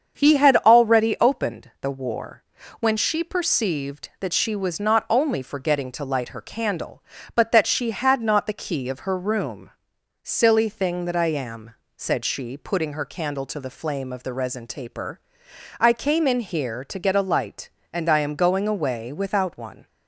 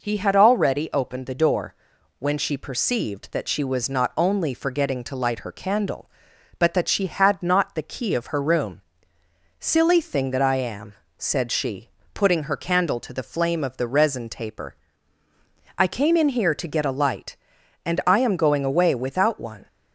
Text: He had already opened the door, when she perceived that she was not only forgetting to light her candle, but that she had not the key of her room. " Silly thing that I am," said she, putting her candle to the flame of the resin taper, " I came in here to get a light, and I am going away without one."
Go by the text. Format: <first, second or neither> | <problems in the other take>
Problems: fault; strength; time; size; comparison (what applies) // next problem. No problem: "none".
second | starts louder than the rest; strong; until 1.2 s; 7 dB // says "war" for "door"; at 1.8 s